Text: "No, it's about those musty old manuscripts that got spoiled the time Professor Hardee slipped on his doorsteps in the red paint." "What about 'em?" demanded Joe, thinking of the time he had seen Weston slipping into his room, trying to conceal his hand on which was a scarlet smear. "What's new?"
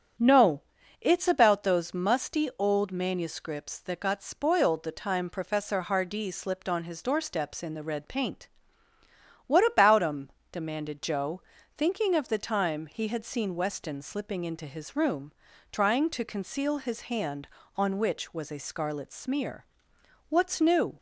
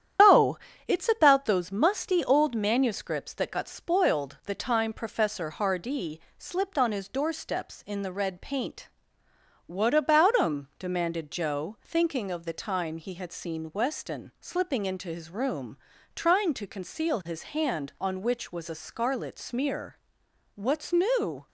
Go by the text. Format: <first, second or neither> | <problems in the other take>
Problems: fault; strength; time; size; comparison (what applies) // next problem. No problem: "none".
first | loses the start of "No"; at 0.1 s; 160 ms // starts louder than the rest; strong; until 1.5 s; 10 dB; strong in the first // pauses between "Hardee" and "slipped"; slight; at 6.1 s; 0.20 s long // pauses between "his" and "hand"; slight; at 17.4 s; 0.16 s long